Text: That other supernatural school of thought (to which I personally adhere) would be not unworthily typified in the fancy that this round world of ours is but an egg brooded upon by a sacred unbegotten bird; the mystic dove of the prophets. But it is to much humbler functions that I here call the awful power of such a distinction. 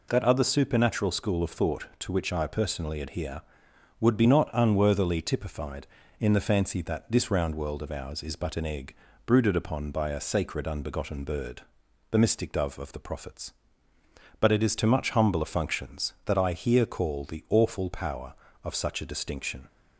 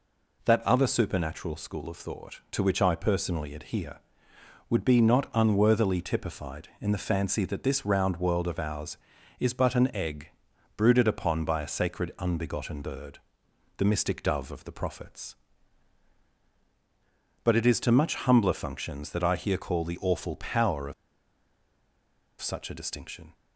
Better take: first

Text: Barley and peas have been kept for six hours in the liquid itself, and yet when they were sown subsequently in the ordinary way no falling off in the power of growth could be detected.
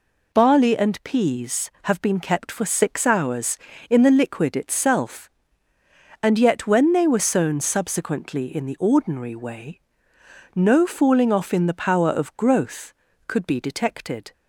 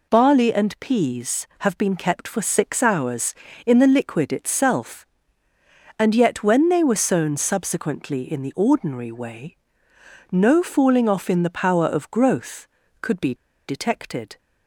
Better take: first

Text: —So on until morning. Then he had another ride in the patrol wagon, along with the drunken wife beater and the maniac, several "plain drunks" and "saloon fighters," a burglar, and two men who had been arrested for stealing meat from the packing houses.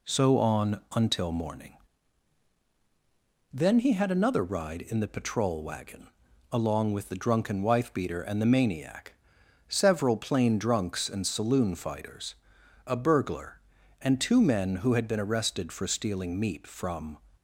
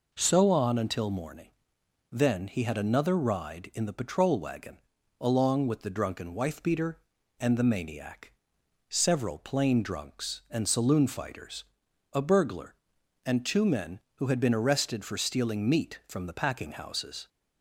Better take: second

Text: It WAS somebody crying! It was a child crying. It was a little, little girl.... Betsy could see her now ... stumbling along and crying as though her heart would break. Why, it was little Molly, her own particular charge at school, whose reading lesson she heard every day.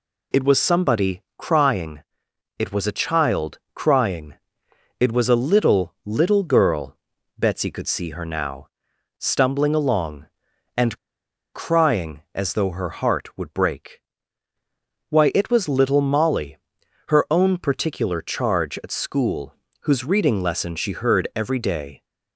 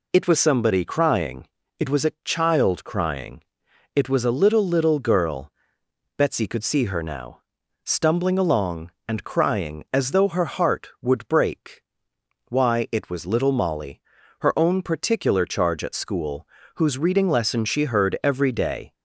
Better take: second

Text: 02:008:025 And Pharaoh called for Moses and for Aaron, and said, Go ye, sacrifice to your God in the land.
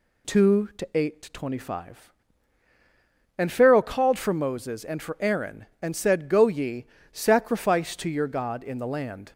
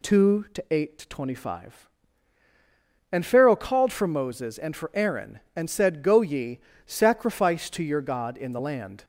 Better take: neither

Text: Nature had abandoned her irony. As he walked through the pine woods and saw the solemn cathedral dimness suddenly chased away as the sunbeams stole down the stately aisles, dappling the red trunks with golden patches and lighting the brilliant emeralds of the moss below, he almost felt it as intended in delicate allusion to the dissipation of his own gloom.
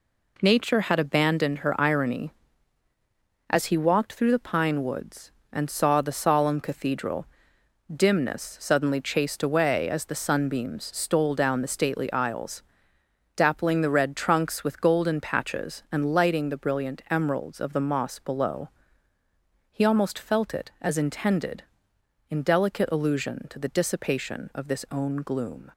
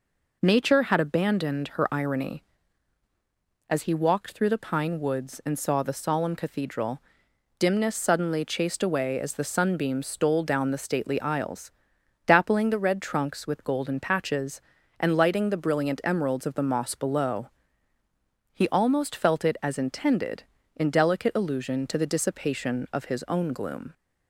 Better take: second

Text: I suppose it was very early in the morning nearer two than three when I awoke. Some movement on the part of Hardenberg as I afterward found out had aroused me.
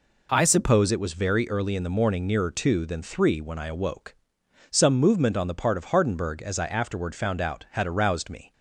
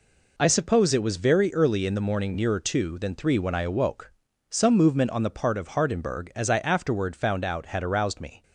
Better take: neither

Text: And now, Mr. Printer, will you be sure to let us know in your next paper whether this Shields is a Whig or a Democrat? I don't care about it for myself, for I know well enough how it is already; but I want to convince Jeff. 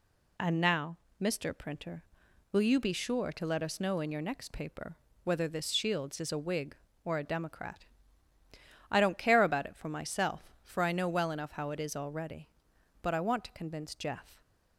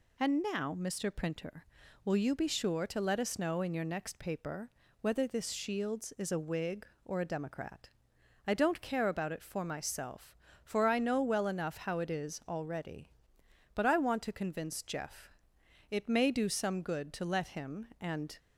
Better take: first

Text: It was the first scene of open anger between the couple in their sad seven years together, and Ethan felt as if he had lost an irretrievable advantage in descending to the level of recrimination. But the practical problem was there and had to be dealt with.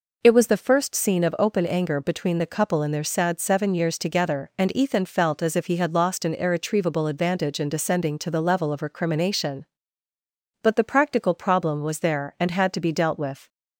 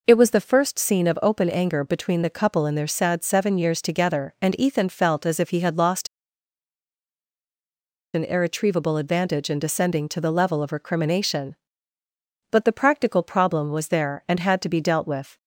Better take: first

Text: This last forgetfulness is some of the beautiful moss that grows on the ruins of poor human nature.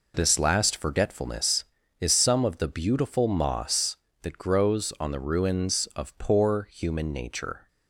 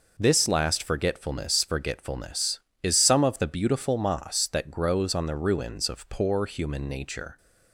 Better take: first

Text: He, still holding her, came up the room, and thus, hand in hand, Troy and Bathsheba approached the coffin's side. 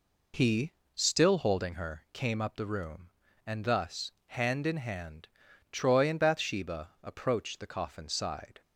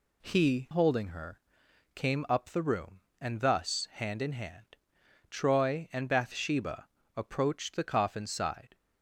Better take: first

